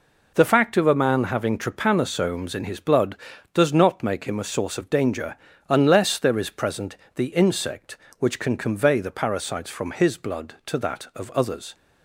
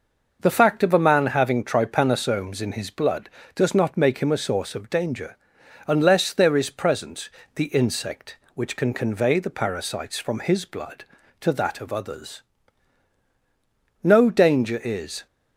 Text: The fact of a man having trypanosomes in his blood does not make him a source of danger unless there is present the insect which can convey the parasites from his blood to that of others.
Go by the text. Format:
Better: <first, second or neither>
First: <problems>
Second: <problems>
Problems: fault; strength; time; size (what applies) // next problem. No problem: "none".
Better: first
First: pauses between "danger" and "unless"; slight; at 5.3 s; 0.32 s long // pauses between "present" and "the"; slight; at 6.9 s; 0.20 s long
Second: starts louder than the rest; noticeable; until 1.4 s; 6 dB // pauses between "danger" and "unless"; noticeable; at 5.3 s; 0.50 s long // pauses between "present" and "the"; slight; at 7.3 s; 0.24 s long // goes on to say "No danger is"; noticeable; from 14.0 s on; 1.2 s long